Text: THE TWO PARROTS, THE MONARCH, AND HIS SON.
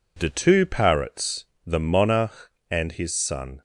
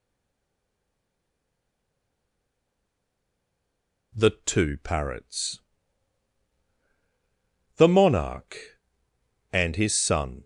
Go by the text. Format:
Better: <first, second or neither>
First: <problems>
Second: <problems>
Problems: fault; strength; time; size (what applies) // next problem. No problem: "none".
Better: first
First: none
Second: stays silent before the first word; strong; until 4.1 s; 4.1 s long